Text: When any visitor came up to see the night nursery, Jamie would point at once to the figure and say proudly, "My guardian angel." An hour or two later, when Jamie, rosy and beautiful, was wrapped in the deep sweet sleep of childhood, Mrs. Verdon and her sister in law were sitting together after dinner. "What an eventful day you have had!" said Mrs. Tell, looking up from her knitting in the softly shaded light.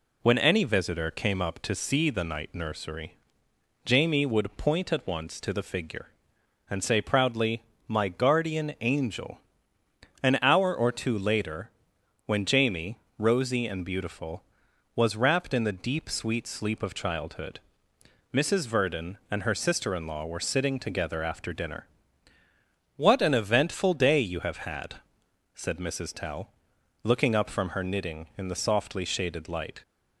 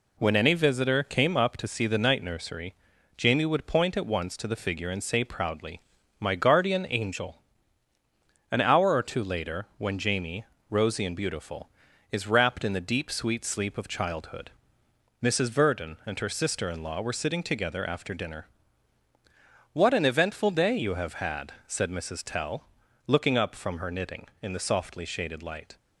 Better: first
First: none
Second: says "is" for "was"; at 12.1 s

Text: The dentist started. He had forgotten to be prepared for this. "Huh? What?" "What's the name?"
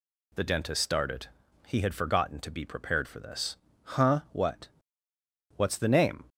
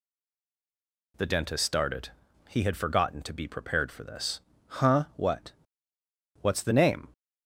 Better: first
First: none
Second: stays silent before the first word; until 1.1 s; 1.1 s long

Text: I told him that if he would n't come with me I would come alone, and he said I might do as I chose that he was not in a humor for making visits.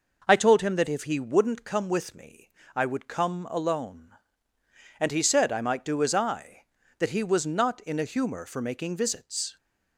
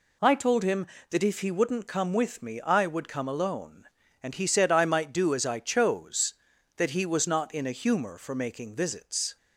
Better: second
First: pauses between "me" and "I"; slight; at 2.4 s; 0.26 s long // skips "chose"; at 6.8 s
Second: none

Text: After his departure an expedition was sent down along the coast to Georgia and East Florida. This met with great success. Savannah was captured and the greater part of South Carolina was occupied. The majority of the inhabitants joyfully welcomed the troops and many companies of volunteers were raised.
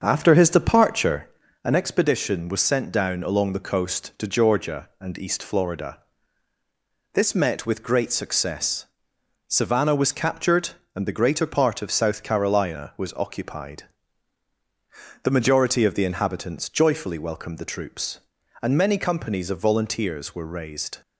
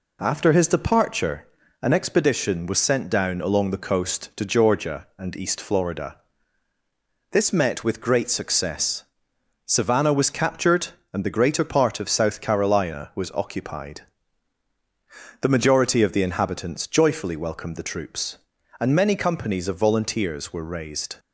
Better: second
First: starts louder than the rest; until 1.4 s; 7 dB // pauses between "departure" and "an"; slight; at 1.2 s; 0.36 s long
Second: pauses between "departure" and "an"; slight; at 1.4 s; 0.36 s long

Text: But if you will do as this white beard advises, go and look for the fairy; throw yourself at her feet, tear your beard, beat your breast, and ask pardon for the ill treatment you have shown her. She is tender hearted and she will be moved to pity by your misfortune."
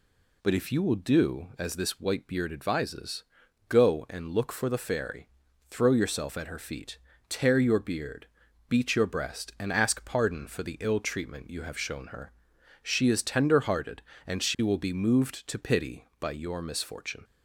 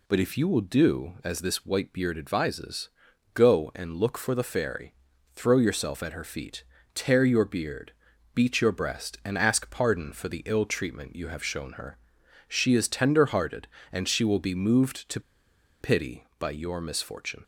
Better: first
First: none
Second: pauses between "to" and "pity"; noticeable; at 15.1 s; 0.60 s long

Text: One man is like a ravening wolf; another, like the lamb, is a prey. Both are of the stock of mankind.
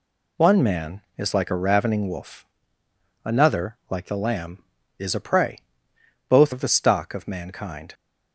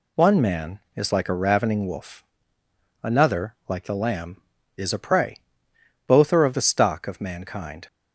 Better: second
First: skips "are"; at 6.5 s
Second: none

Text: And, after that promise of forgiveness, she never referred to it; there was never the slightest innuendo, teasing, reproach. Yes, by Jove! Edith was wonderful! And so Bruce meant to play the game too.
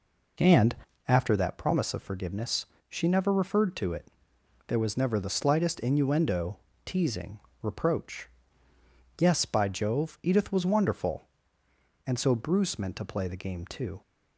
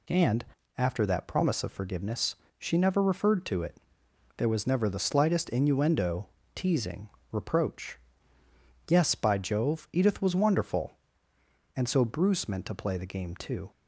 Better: second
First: starts louder than the rest; noticeable; until 1.4 s; 4 dB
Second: none

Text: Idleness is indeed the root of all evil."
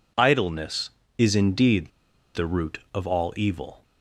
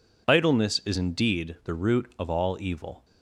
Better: second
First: pauses between "indeed" and "the"; at 1.8 s; 0.44 s long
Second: none

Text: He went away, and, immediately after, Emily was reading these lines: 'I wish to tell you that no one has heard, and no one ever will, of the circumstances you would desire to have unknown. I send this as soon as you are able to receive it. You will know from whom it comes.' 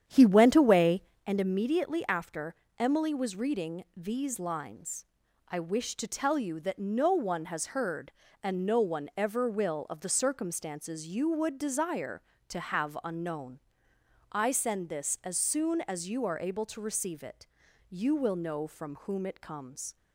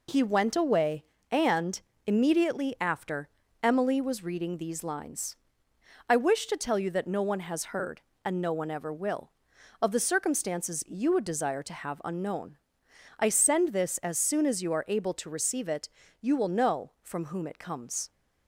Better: second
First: starts louder than the rest; strong; until 1.3 s; 9.5 dB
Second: none

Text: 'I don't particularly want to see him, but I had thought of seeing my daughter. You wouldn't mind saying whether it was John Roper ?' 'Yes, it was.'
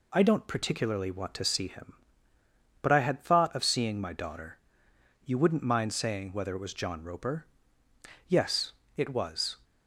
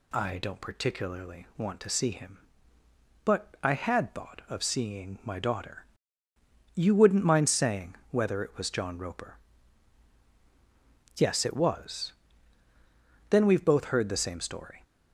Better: first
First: none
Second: pauses between "saying" and "whether"; slight; at 7.9 s; 0.16 s long // goes on to say "Then we've both heard the same story"; from 13.2 s on; 1.5 s long

